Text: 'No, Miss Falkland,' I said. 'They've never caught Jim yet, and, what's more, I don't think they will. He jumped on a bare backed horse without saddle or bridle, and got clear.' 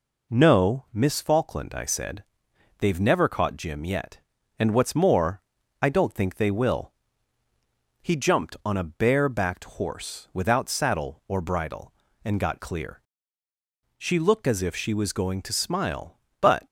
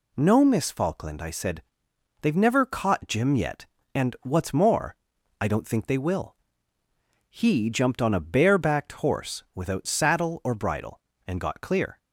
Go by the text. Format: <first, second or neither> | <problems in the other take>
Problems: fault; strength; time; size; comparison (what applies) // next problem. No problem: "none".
second | goes on to say "She looked as if she was going to smile but"; strong; from 13.9 s on; 2.6 s long